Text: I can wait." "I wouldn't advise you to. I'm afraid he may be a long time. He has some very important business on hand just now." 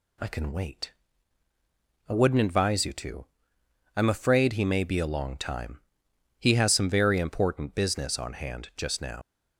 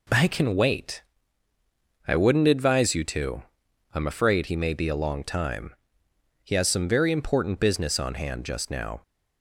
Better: second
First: leaves "now" unfinished; at 9.2 s; 95 ms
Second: none

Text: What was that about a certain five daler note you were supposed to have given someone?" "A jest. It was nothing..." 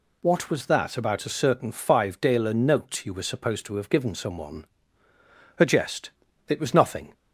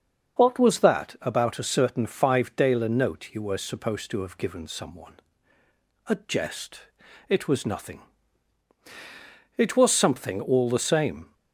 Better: first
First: none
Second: starts louder than the rest; until 1.4 s; 6.5 dB // goes on to say "It was something all the same"; strong; from 9.5 s on; 1.7 s long

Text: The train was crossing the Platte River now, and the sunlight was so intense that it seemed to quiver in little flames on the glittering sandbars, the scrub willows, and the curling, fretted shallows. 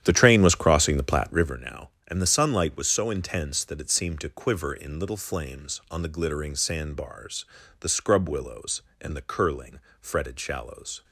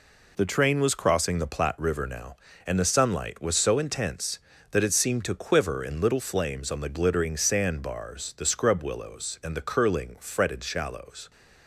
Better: second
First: starts louder than the rest; strong; until 1.5 s; 10.5 dB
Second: none

